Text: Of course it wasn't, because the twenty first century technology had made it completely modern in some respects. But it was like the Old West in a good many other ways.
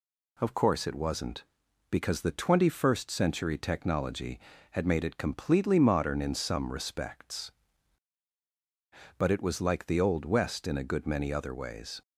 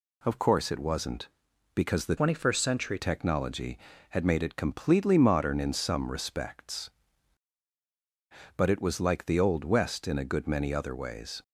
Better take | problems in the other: first | changes voice from "twenty" to "century"; from 2.1 to 2.9 s; 0.8 s long

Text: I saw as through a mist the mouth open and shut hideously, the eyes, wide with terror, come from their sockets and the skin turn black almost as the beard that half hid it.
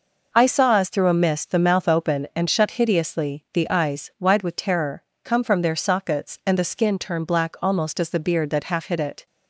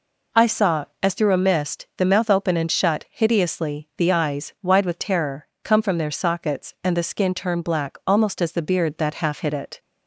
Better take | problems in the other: neither | none

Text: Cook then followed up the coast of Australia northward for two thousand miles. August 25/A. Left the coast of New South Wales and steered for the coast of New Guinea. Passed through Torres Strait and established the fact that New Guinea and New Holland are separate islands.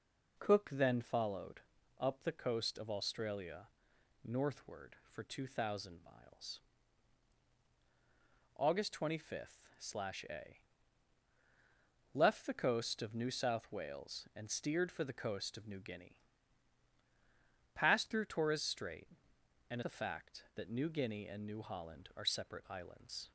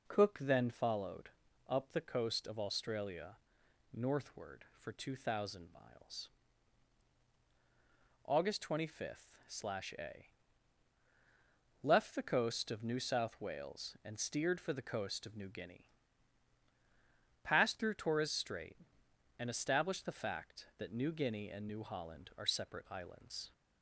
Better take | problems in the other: second | pauses between "followed" and "up"; at 1.6 s; 0.38 s long; also in the second // pauses between "Australia" and "northward"; noticeable; at 3.6 s; 0.54 s long; noticeable in the second // skips "established"; at 19.8 s

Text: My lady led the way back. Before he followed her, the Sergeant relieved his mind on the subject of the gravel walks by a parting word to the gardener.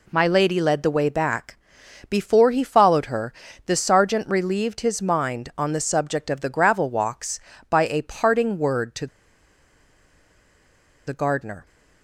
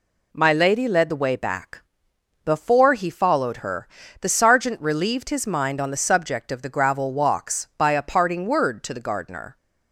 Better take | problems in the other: second | pauses between "to" and "the"; strong; at 9.0 s; 2.0 s long

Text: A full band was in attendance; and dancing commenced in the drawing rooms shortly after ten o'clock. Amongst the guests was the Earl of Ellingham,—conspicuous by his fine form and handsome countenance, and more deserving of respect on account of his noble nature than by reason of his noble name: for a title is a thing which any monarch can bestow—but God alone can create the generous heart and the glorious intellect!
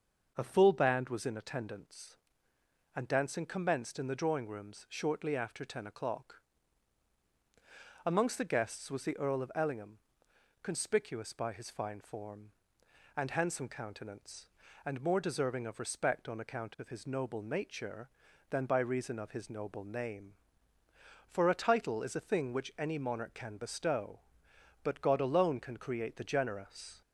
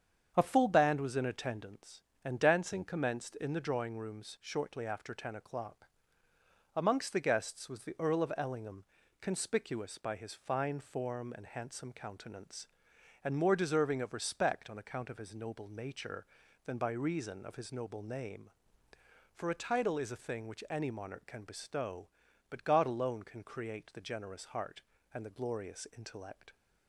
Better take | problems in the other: second | starts louder than the rest; until 1.3 s; 6.5 dB; strong in the second // stops before "heart and the glorious intellect"; at 27.0 s

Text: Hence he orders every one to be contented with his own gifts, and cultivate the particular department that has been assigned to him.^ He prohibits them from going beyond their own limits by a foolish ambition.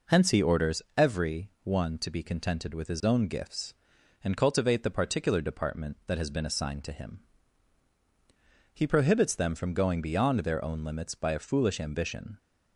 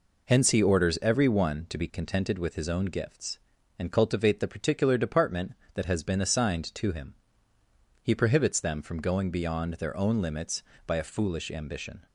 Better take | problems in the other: neither | none

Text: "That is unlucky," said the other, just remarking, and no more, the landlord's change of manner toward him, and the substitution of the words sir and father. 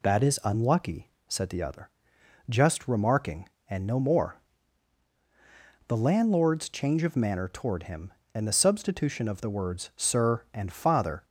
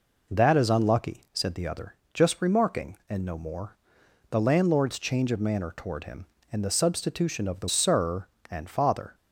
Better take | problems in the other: first | skips "words"; at 7.6 s

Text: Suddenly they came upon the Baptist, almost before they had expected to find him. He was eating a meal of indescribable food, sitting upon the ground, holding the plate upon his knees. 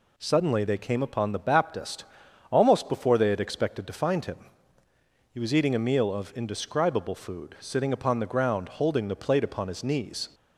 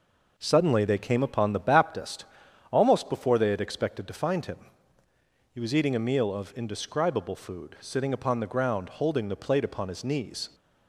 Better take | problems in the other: first | starts louder than the rest; noticeable; until 2.1 s; 4.5 dB

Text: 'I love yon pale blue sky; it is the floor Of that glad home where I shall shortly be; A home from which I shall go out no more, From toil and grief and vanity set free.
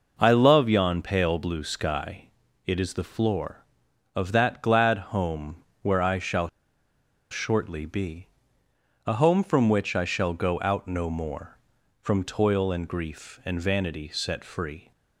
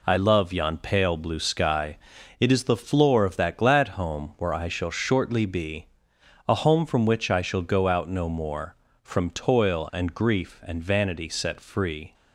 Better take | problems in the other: second | pauses between "glad" and "home"; slight; at 4.9 s; 0.16 s long // pauses between "home" and "where"; slight; at 5.5 s; 0.26 s long // pauses between "shall" and "shortly"; noticeable; at 6.4 s; 0.83 s long

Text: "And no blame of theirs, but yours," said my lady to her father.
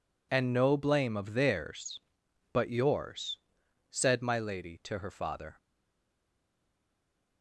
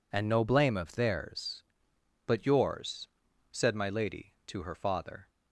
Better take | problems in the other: second | stays silent after the last word; noticeable; from 5.5 s on; 1.9 s long

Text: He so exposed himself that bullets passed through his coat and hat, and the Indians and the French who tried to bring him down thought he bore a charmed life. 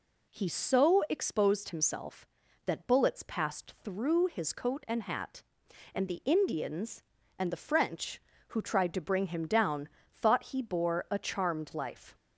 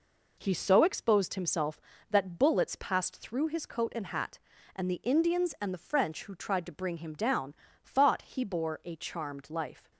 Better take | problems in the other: neither | pauses between "down" and "thought"; slight; the same in both

